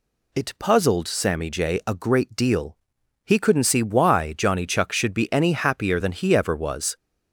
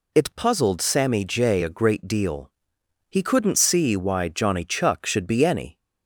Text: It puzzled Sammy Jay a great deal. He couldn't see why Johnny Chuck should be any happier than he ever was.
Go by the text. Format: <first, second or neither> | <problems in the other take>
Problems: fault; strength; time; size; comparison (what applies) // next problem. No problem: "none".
first | stops before "happier than he ever was"; at 5.7 s